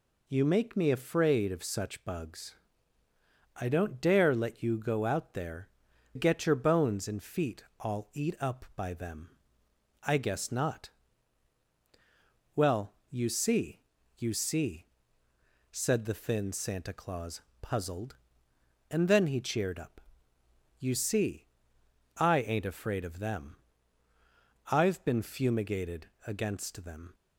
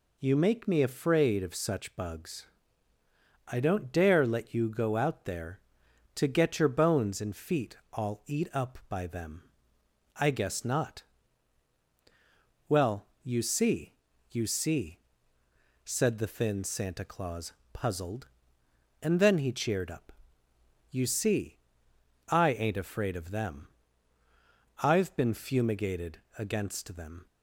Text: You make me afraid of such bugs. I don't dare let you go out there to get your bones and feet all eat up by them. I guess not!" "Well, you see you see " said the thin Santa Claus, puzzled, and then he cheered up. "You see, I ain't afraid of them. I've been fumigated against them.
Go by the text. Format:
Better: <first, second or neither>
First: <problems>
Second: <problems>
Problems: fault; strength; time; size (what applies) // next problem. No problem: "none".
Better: second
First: skips "to"; at 5.9 s // pauses between "feet" and "all"; slight; at 7.6 s; 0.16 s long // pauses between "see" and "you"; at 13.8 s; 0.38 s long // pauses between "fumigated" and "against"; slight; at 26.1 s; 0.16 s long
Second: pauses between "feet" and "all"; slight; at 7.7 s; 0.16 s long // pauses between "see" and "you"; at 13.9 s; 0.38 s long // pauses between "fumigated" and "against"; slight; at 26.2 s; 0.16 s long